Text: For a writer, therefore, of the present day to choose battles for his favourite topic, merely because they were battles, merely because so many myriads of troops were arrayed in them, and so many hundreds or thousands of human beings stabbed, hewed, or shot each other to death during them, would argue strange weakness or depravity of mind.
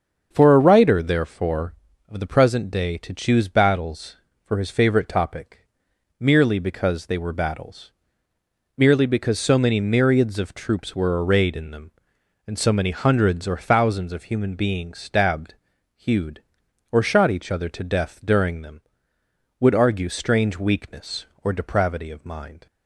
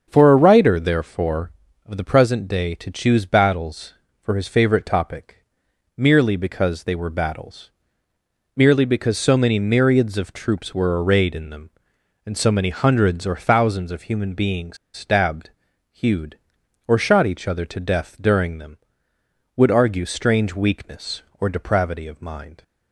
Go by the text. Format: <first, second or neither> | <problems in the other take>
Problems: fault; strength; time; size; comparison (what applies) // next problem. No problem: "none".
first | starts louder than the rest; until 1.1 s; 7 dB; also in the first // pauses between "beings" and "stabbed"; slight; at 14.7 s; 0.17 s long